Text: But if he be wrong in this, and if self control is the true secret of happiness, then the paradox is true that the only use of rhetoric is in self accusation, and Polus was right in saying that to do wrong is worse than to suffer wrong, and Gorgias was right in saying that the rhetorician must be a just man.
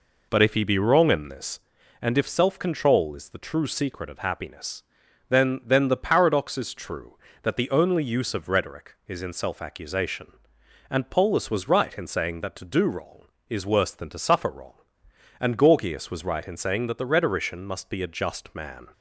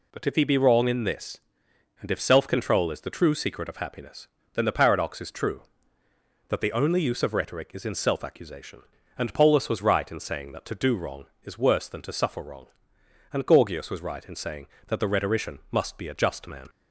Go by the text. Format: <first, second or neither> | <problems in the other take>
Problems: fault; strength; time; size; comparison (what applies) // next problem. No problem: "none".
second | says "then" twice; at 5.6 s